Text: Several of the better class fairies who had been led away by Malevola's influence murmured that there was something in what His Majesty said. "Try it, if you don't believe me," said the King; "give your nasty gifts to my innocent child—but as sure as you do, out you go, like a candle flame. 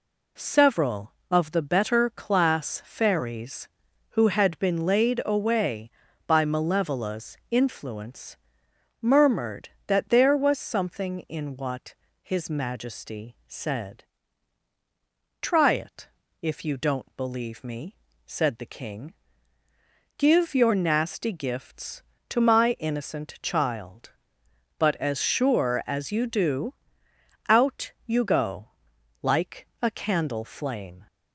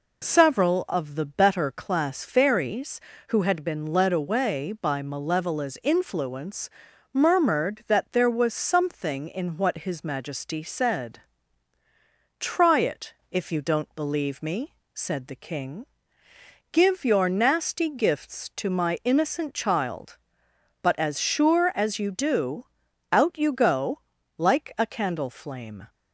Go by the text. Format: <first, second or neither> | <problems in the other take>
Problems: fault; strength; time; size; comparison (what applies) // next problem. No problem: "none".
second | says "laid" for "led"; at 4.8 s // pauses between "influence" and "murmured"; noticeable; at 8.3 s; 0.64 s long; also in the second // pauses between "what" and "His"; slight; at 11.9 s; 0.26 s long // pauses between "like" and "a"; slight; at 29.6 s; 0.16 s long